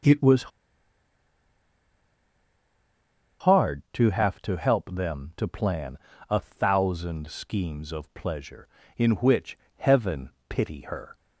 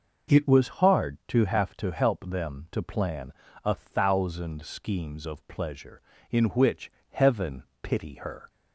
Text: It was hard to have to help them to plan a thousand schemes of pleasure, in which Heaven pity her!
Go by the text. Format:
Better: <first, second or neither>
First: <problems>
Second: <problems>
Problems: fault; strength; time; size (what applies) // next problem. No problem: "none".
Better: second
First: pauses between "was" and "hard"; strong; at 0.5 s; 2.9 s long // pauses between "plan" and "a"; slight; at 5.9 s; 0.32 s long // pauses between "which" and "Heaven"; slight; at 9.5 s; 0.20 s long // pauses between "Heaven" and "pity"; slight; at 10.2 s; 0.18 s long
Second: pauses between "plan" and "a"; slight; at 3.3 s; 0.32 s long // pauses between "which" and "Heaven"; slight; at 6.9 s; 0.20 s long // pauses between "Heaven" and "pity"; slight; at 7.6 s; 0.18 s long